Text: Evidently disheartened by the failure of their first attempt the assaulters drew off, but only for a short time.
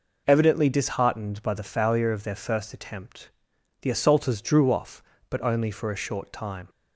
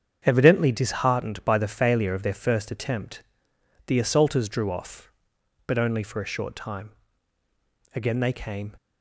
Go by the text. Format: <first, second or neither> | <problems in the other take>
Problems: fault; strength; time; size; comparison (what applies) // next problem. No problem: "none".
first | starts louder than the rest; strong; until 1.2 s; 8 dB // pauses between "attempt" and "the"; noticeable; at 3.2 s; 0.64 s long; noticeable in the first // goes on to say "Again they came"; noticeable; from 7.9 s on; 0.82 s long